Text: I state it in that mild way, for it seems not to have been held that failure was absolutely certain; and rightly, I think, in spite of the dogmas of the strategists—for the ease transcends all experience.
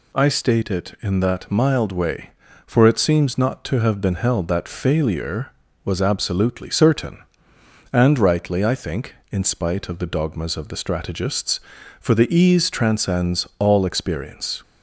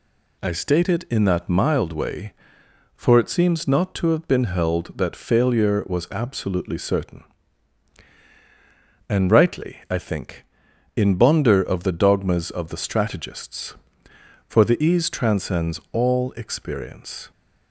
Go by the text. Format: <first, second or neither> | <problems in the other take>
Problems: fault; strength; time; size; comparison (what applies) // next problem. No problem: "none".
first | says "bonder" for "spite"; at 11.1 s